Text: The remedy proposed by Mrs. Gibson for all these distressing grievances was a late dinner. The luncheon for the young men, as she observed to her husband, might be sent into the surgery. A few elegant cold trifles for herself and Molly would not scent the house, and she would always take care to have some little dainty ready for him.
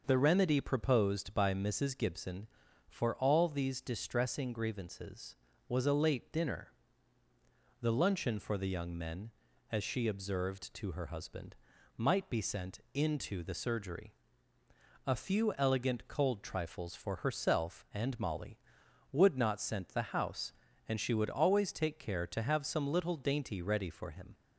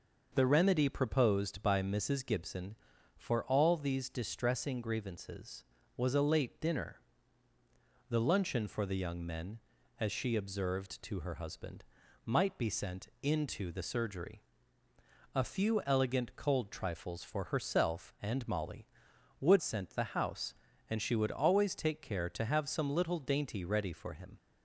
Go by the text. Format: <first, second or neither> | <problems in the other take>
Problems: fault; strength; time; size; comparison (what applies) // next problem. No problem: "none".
first | skips "not"; at 19.6 s